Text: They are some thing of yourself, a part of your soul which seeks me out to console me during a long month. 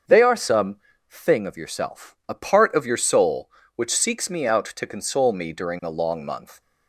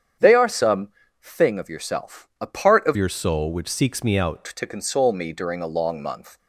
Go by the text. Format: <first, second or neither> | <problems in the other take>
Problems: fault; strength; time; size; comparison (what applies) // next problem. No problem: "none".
first | starts louder than the rest; strong; until 1.5 s; 8.5 dB; also in the first // pauses between "some" and "thing"; slight; at 0.8 s; 0.34 s long; slight in the first // changes voice from "your" to "out"; from 2.9 to 4.4 s; 1.5 s long